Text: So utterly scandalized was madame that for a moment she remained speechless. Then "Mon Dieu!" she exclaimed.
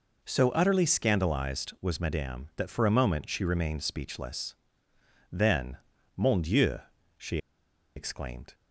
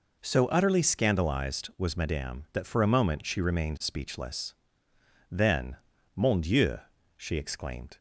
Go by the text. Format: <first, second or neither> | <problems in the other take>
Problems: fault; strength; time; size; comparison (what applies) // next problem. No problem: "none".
second | pauses between "Then" and "Mon"; at 5.7 s; 0.38 s long; also in the second // pauses between "she" and "exclaimed"; noticeable; at 7.3 s; 0.57 s long